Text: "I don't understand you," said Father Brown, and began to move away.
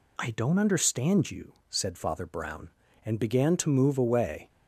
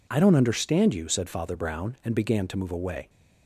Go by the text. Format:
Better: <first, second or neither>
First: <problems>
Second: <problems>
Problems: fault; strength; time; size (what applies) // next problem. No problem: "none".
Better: neither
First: none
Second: none